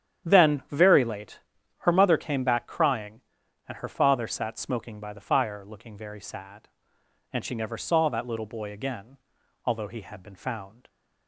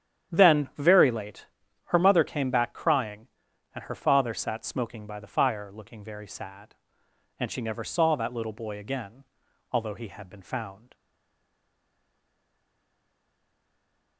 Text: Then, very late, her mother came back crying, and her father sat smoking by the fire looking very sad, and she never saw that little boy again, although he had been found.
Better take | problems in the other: first | starts louder than the rest; strong; until 1.3 s; 9.5 dB; strong in the first // stays silent after the last word; strong; from 10.9 s on; 3.2 s long

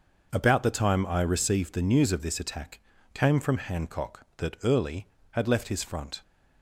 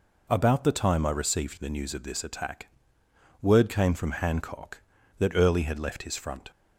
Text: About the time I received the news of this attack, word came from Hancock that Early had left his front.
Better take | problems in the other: second | skips "word"; at 2.9 s

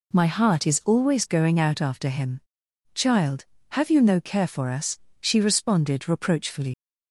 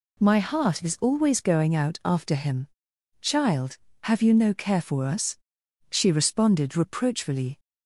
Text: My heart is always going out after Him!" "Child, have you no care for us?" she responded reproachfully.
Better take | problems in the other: second | leaves "reproachfully" unfinished; at 6.7 s; 80 ms

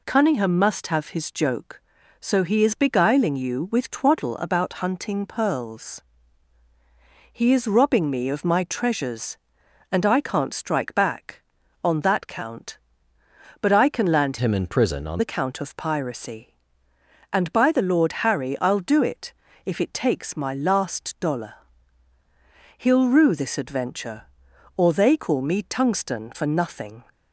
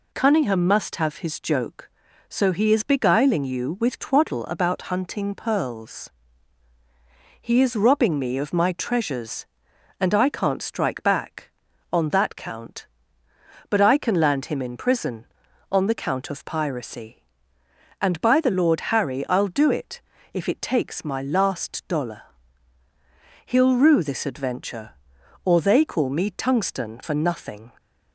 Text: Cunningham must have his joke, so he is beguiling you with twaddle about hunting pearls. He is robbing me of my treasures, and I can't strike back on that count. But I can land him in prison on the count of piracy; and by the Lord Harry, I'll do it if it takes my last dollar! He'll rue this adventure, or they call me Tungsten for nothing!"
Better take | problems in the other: second | changes voice from "him" to "on"; from 14.3 to 15.2 s; 0.9 s long // pauses between "it" and "if"; slight; at 19.3 s; 0.34 s long; slight in the second

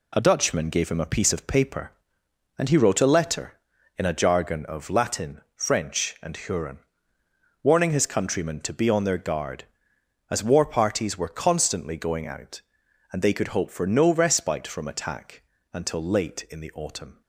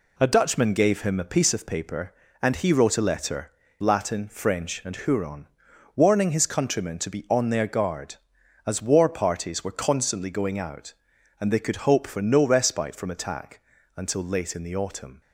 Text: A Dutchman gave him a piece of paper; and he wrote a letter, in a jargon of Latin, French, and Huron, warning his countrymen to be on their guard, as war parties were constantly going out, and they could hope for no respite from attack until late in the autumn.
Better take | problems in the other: first | skips "in a jargon of"; at 3.6 s // pauses between "attack" and "until"; slight; at 13.6 s; 0.34 s long; slight in the first

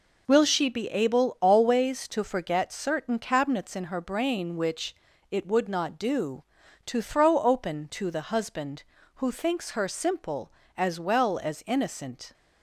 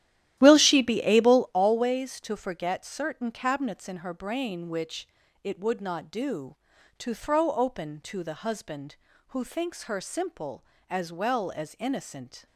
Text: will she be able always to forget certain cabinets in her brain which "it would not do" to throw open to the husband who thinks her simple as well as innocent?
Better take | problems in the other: first | starts louder than the rest; strong; until 1.6 s; 12.5 dB // pauses between "which" and "it"; slight; at 5.0 s; 0.36 s long; slight in the first

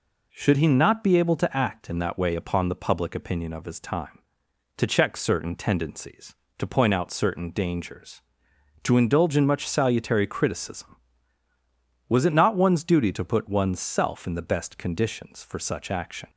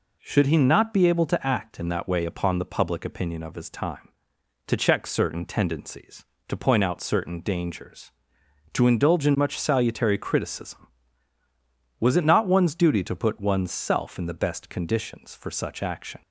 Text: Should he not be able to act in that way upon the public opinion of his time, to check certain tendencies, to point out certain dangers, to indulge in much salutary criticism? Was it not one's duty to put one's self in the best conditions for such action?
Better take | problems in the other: neither | none

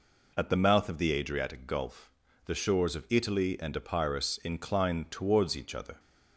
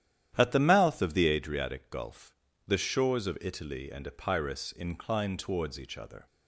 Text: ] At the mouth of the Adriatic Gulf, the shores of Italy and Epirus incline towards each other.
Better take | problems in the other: first | starts louder than the rest; strong; until 1.4 s; 11 dB

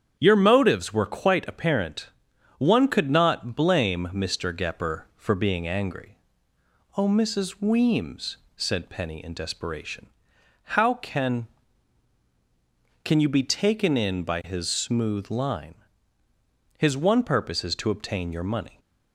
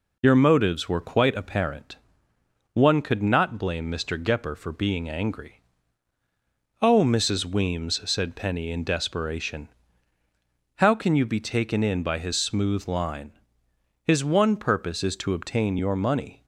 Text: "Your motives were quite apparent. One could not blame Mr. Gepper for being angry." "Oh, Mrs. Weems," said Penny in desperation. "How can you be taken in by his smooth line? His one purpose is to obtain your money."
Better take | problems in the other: second | starts louder than the rest; strong; until 1.1 s; 8 dB // says "can" twice; at 13.0 s

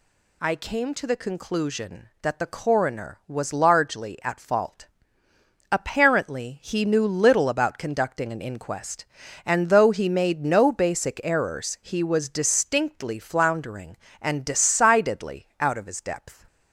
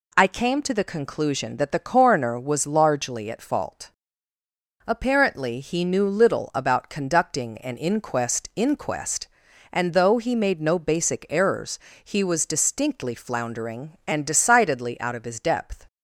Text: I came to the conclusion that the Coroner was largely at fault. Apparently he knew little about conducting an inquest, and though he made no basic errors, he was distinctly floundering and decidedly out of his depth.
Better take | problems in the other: first | says "inquest" twice; at 8.5 s

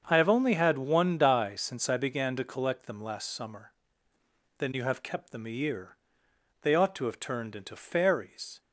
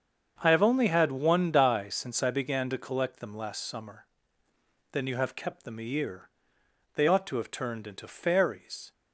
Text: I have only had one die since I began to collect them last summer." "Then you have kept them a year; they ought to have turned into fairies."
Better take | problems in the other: neither | starts louder than the rest; the same in both

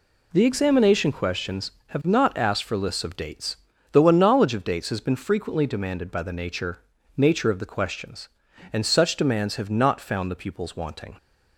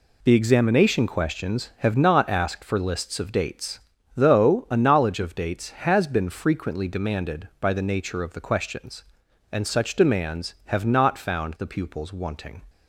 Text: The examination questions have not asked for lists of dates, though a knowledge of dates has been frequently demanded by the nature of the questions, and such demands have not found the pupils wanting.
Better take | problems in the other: second | says "nature" twice; at 7.1 s

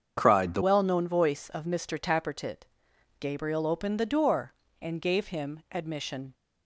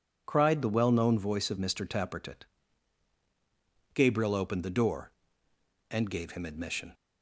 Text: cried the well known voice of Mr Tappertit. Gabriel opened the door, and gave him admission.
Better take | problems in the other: second | starts louder than the rest; strong; until 1.1 s; 7.5 dB // changes voice at "well"; from 0.6 s on; 5.7 s long

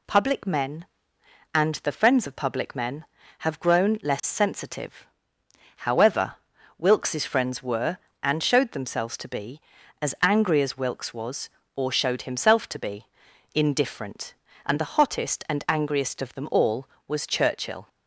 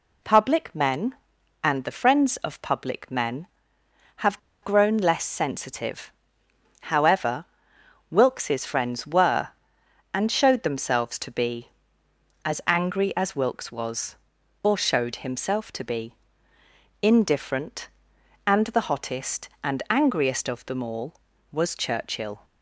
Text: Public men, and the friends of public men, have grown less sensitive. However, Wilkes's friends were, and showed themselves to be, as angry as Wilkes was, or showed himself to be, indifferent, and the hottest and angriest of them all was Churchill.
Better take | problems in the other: first | pauses between "have" and "grown"; slight; at 4.3 s; 0.22 s long

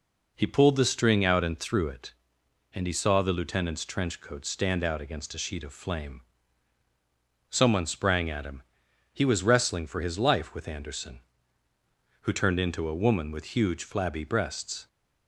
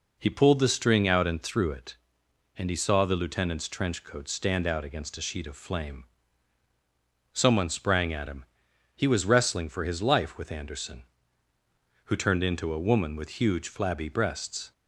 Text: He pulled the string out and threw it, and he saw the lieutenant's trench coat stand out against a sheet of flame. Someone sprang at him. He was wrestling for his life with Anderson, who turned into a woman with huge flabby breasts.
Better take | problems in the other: neither | none

